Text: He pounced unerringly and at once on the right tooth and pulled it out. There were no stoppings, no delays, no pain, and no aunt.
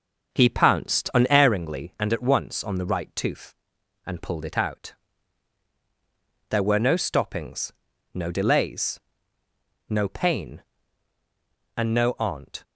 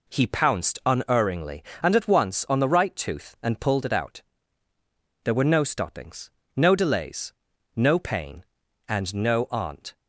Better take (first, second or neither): second